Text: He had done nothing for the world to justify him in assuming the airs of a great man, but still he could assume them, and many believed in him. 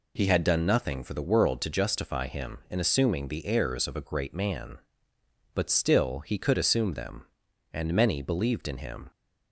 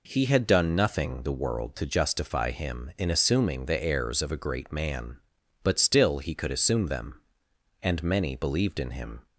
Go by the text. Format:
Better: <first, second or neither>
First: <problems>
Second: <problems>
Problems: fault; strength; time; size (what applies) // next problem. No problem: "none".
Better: first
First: none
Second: skips "for"; at 1.2 s